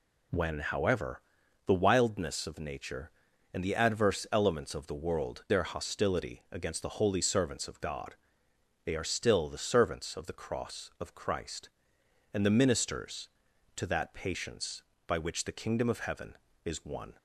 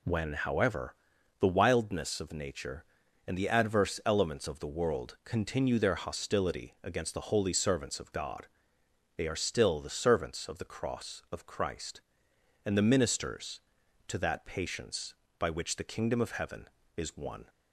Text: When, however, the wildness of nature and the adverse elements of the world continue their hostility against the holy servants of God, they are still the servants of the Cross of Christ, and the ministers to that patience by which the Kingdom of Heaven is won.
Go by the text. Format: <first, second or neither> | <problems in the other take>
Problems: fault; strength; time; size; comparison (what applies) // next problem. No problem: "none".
second | skips "continue"; at 5.4 s